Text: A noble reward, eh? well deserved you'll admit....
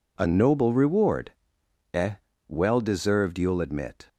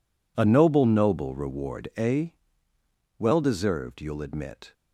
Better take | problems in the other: first | says "noble" twice; at 0.8 s

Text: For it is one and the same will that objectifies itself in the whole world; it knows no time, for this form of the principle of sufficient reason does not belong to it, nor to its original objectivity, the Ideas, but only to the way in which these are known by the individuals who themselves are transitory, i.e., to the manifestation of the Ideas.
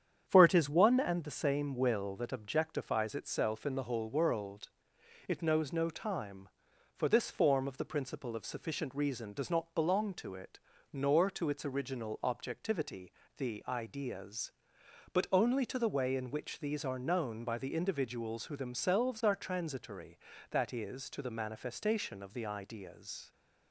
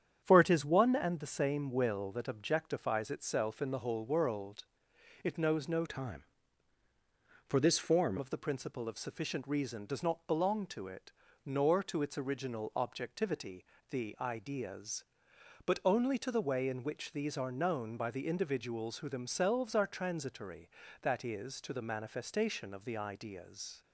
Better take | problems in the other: first | starts louder than the rest; strong; until 1.2 s; 8.5 dB; strong in the first // changes voice from "time" to "form"; from 5.8 to 8.1 s; 2.3 s long

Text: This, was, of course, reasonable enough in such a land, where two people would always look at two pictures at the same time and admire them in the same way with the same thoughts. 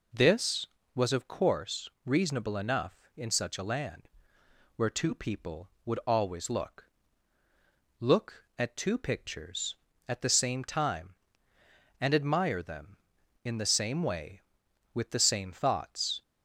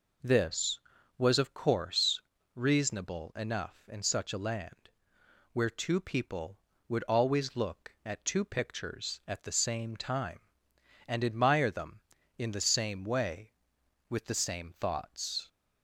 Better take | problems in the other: second | says "look" twice; at 7.9 s

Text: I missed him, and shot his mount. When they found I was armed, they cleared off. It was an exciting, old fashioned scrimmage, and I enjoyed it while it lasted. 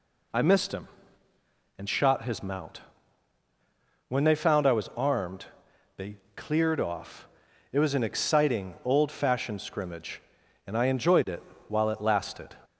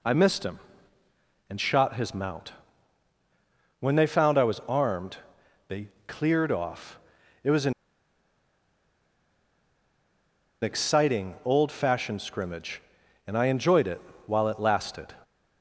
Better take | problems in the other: first | pauses between "they" and "cleared"; slight; at 5.8 s; 0.20 s long; slight in the first // pauses between "an" and "exciting"; strong; at 7.7 s; 2.8 s long // pauses between "it" and "while"; slight; at 14.0 s; 0.26 s long; slight in the first

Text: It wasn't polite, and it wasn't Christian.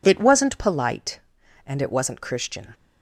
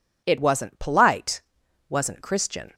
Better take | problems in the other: first | skips "and it"; at 1.6 s

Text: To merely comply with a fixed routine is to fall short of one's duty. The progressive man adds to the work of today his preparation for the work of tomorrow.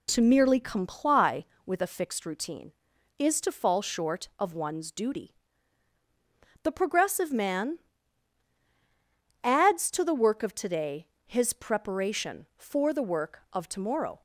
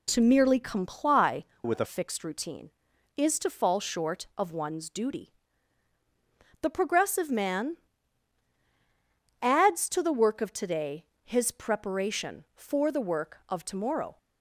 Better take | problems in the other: first | changes voice from "with" to "a"; from 1.6 to 1.8 s; 0.2 s long // pauses between "man" and "adds"; strong; at 7.7 s; 1.6 s long; strong in the first // pauses between "today" and "his"; slight; at 11.0 s; 0.22 s long; slight in the first

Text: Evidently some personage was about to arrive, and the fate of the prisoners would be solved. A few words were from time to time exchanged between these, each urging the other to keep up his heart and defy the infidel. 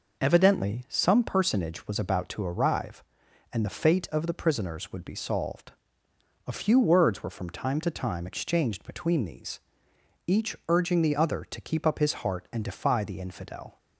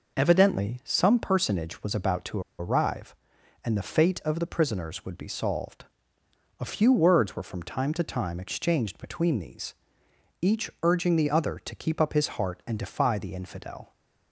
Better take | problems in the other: first | pauses between "to" and "arrive"; slight; at 2.4 s; 0.18 s long

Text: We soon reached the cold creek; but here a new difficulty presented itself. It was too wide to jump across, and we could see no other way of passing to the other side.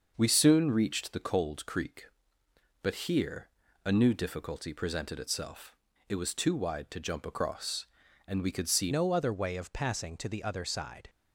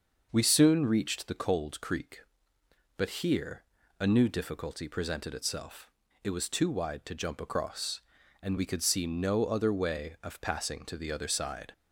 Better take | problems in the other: second | starts louder than the rest; until 1.1 s; 6 dB; also in the second // pauses between "here" and "a"; slight; at 3.4 s; 0.36 s long; slight in the second // changes voice at "no"; from 8.9 s on; 2.1 s long

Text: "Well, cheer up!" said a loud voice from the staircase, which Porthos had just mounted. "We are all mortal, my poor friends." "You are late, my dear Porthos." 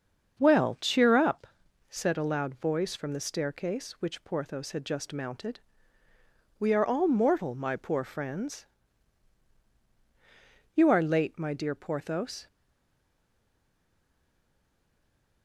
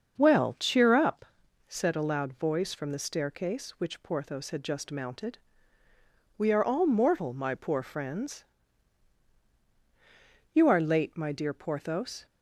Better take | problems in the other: second | starts louder than the rest; until 1.4 s; 7 dB; also in the second // stays silent after the last word; strong; from 12.4 s on; 3.0 s long

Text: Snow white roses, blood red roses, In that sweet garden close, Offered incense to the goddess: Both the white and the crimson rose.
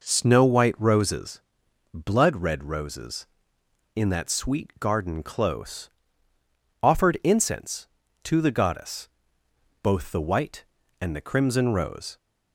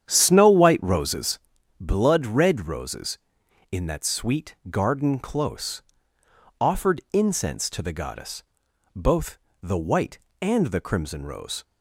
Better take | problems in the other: first | starts louder than the rest; strong; until 1.4 s; 9 dB // pauses between "sweet" and "garden"; slight; at 4.5 s; 0.16 s long // pauses between "Both" and "the"; slight; at 9.3 s; 0.24 s long

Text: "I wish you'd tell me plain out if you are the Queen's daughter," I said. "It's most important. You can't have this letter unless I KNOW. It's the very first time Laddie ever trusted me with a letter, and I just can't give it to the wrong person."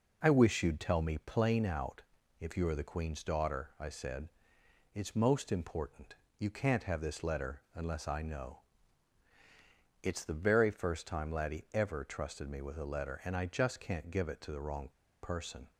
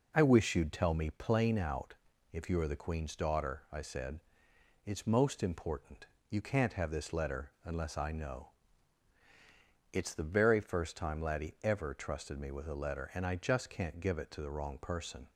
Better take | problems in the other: second | pauses between "out" and "if"; at 2.0 s; 0.38 s long; also in the second // pauses between "wrong" and "person"; slight; at 14.8 s; 0.32 s long

